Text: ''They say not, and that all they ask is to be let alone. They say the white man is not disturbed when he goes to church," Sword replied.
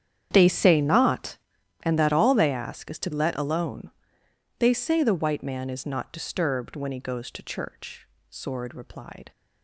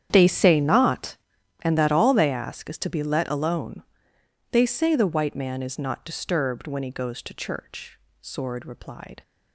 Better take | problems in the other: second | starts louder than the rest; strong; until 1.3 s; 9 dB; strong in the second // skips "be"; at 3.1 s

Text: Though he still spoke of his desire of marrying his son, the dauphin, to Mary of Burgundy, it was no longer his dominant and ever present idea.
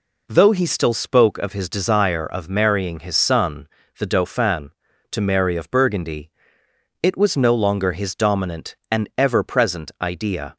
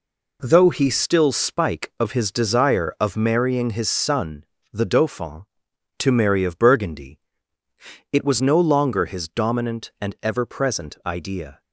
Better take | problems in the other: first | says "spike" for "spoke"; at 1.3 s

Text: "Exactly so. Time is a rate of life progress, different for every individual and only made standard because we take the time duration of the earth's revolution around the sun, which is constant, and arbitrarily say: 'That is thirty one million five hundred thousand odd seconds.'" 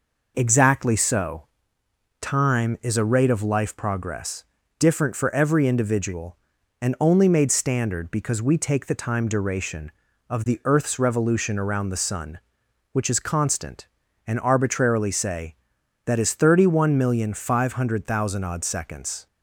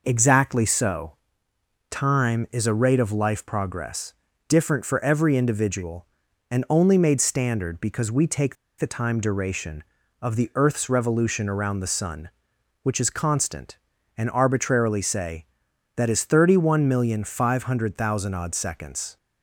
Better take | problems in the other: first | pauses between "take" and "the"; slight; at 8.5 s; 0.23 s long

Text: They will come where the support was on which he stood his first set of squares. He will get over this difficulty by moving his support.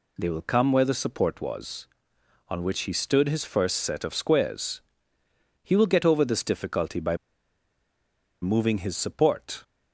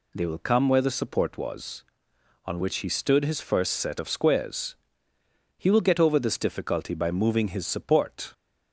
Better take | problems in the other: second | pauses between "by" and "moving"; strong; at 7.1 s; 1.2 s long

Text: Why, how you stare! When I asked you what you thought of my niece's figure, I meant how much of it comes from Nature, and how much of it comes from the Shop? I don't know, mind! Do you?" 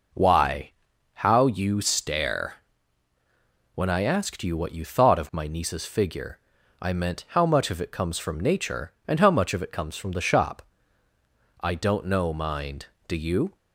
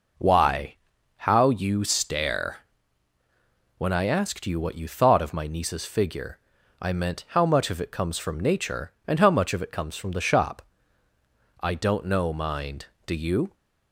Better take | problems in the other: neither | none

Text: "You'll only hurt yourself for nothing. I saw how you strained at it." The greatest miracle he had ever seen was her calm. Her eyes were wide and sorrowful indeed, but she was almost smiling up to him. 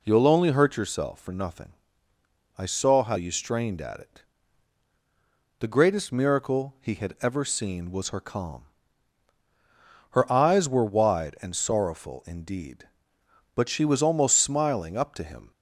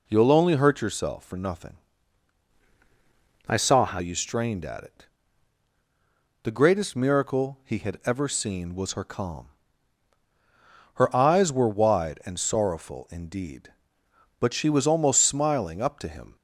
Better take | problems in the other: first | changes voice from "I" to "how"; from 3.4 to 3.9 s; 0.5 s long

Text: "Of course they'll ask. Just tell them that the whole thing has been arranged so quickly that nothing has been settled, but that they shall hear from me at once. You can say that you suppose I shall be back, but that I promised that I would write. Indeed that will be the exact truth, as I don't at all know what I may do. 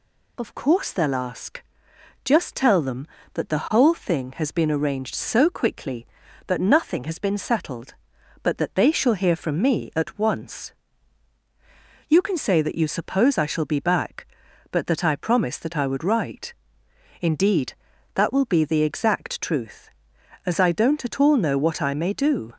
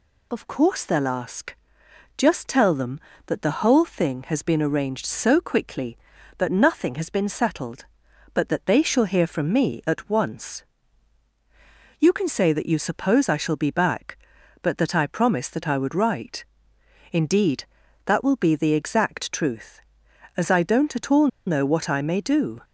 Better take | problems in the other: first | pauses between "all" and "know"; slight; at 21.2 s; 0.19 s long

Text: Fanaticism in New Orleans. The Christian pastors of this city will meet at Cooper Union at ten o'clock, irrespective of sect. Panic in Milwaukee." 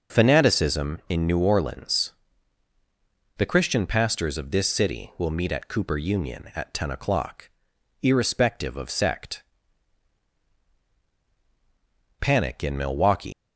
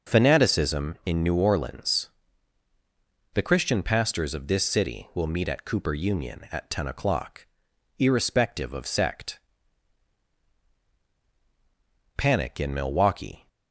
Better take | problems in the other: second | leaves "Milwaukee" unfinished; at 13.3 s; 185 ms

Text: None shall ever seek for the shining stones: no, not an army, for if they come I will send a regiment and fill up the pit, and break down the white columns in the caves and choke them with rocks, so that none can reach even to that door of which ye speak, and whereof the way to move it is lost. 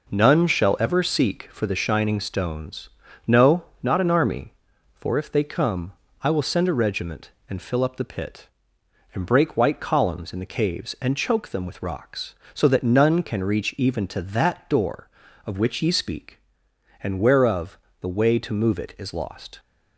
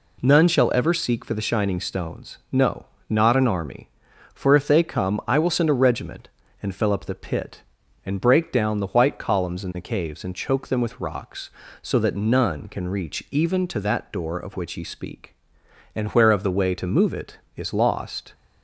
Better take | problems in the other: second | pauses between "come" and "I"; slight; at 5.9 s; 0.30 s long // skips "down the"; at 9.5 s // pauses between "whereof" and "the"; slight; at 17.7 s; 0.22 s long

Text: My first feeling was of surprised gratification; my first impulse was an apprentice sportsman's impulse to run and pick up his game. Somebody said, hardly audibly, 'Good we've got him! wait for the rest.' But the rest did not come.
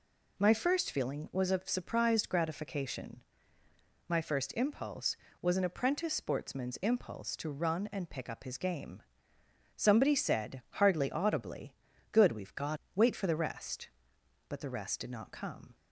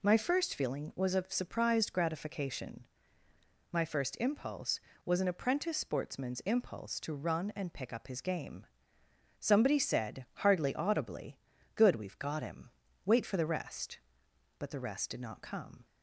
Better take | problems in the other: second | skips "him"; at 12.8 s

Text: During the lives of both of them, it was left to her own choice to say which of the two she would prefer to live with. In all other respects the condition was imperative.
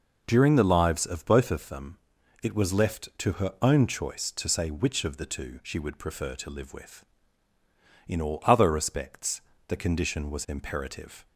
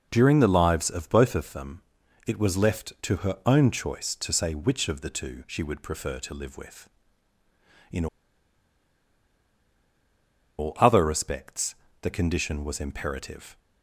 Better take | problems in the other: first | pauses between "In" and "all"; strong; at 8.0 s; 2.5 s long // pauses between "respects" and "the"; slight; at 11.7 s; 0.24 s long; slight in the first

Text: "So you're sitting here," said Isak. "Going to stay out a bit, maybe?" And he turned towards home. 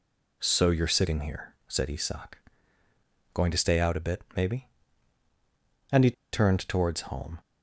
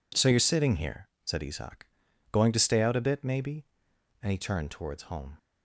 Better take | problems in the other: second | pauses between "he" and "turned"; slight; at 6.1 s; 0.20 s long

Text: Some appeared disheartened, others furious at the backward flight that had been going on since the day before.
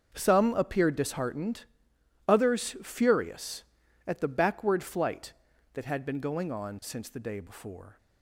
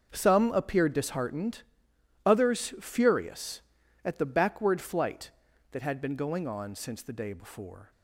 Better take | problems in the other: neither | starts louder than the rest; the same in both

